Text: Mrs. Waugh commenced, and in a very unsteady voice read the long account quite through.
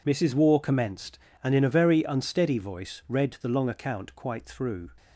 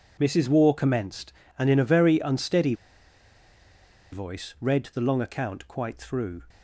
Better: first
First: none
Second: pauses between "unsteady" and "voice"; strong; at 2.7 s; 1.3 s long

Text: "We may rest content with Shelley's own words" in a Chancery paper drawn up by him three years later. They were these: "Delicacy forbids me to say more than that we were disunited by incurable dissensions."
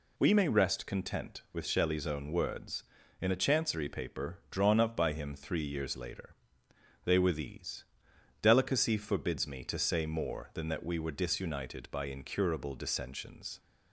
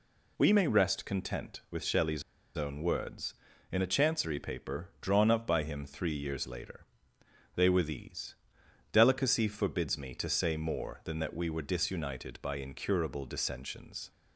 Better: first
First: none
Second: pauses between "Shelley's" and "own"; slight; at 2.2 s; 0.35 s long

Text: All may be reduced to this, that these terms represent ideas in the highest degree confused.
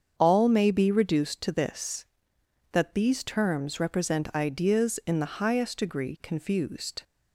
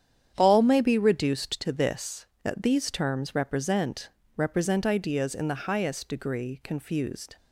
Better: first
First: starts louder than the rest; strong; until 1.1 s; 7.5 dB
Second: starts louder than the rest; strong; until 1.3 s; 9 dB // says "represent" twice; at 4.3 s

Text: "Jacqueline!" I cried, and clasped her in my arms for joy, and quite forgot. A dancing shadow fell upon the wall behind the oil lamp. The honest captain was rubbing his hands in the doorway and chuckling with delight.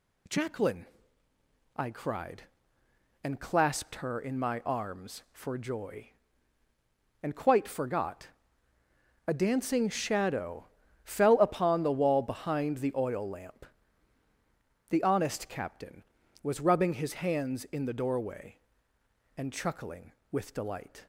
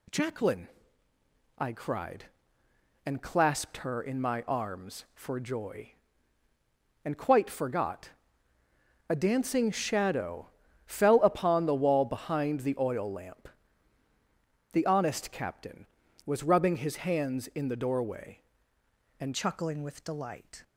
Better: first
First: pauses between "shadow" and "fell"; at 10.6 s; 0.38 s long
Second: pauses between "shadow" and "fell"; at 10.4 s; 0.38 s long // changes voice at "chuckling"; from 19.3 s on; 1.3 s long

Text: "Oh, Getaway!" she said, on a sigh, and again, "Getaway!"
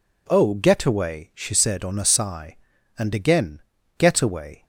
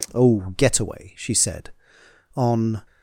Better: first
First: none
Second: stops before "a sigh and again Getaway"; at 2.8 s

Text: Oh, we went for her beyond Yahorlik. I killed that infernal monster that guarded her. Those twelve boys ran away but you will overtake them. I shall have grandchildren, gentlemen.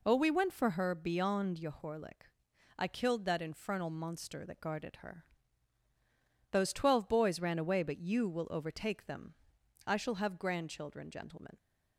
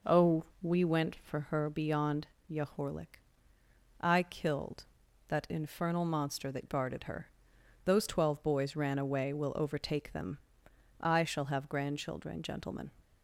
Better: first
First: none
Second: pauses between "beyond" and "Yahorlik"; slight; at 2.2 s; 0.26 s long // skips "but you"; at 9.3 s

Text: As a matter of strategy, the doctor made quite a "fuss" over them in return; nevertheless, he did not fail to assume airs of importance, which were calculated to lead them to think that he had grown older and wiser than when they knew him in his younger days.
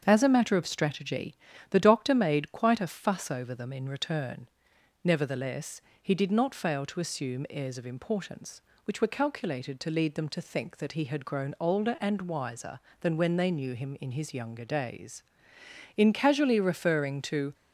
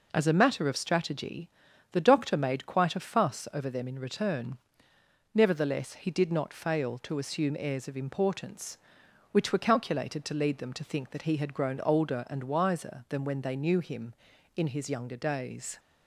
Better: second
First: starts louder than the rest; until 1.0 s; 7 dB // goes on to say "In casually referring to"; from 15.9 s on; 1.5 s long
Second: none

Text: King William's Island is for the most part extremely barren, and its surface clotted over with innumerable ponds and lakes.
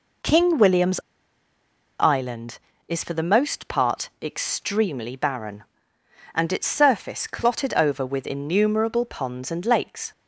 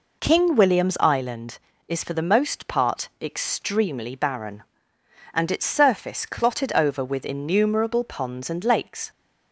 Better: second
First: pauses between "William's" and "Island"; at 0.9 s; 0.99 s long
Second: none

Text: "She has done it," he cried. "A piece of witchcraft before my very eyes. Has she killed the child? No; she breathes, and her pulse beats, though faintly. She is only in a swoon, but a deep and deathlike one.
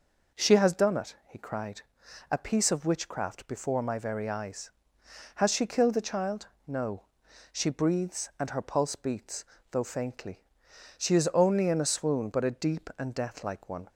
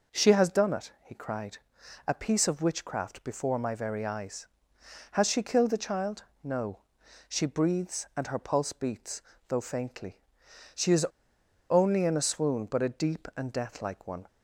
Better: first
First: none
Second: pauses between "is" and "only"; noticeable; at 11.0 s; 0.65 s long

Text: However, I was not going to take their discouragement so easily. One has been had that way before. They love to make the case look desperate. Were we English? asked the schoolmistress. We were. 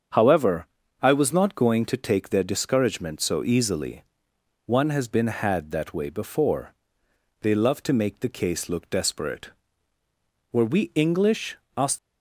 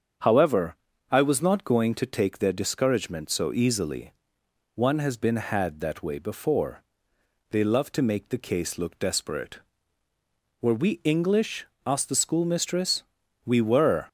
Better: second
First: starts louder than the rest; strong; until 1.4 s; 7.5 dB // stops before "the schoolmistress We were"; at 11.9 s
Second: starts louder than the rest; strong; until 1.5 s; 7.5 dB

